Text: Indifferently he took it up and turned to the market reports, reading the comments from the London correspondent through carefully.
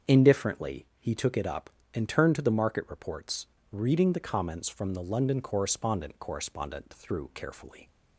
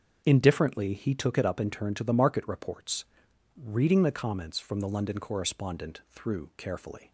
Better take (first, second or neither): second